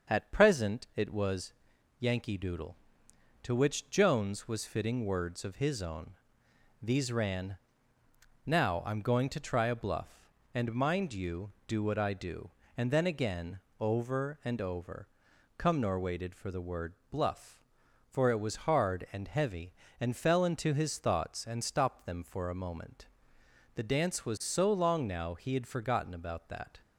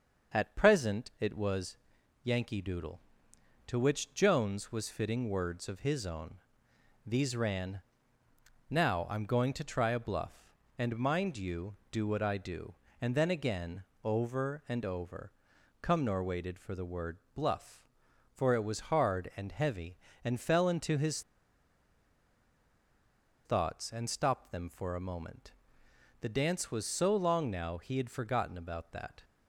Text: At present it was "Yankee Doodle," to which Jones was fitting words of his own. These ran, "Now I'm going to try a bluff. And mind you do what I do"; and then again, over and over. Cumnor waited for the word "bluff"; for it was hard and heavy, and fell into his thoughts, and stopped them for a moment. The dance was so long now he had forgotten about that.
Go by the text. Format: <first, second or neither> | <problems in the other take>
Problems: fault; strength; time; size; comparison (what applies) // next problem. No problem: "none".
first | starts louder than the rest; until 1.4 s; 6.5 dB; also in the first // pauses between "was" and "Yankee"; noticeable; at 1.7 s; 0.46 s long; noticeable in the first // pauses between "word" and "bluff"; slight; at 17.1 s; 0.16 s long; slight in the first // pauses between "his" and "thoughts"; strong; at 21.2 s; 2.2 s long